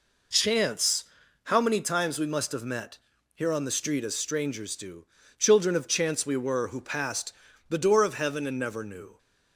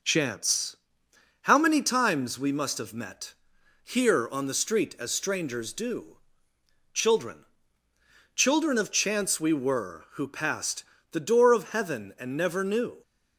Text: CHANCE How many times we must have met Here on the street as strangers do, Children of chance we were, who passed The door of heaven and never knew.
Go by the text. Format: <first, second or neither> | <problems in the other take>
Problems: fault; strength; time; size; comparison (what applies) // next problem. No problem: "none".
first | pauses between "CHANCE" and "How"; noticeable; at 0.7 s; 0.66 s long; also in the first // pauses between "met" and "Here"; noticeable; at 3.3 s; 0.50 s long; slight in the first // says "Children" twice; at 8.3 s // pauses between "passed" and "The"; slight; at 10.8 s; 0.28 s long; slight in the first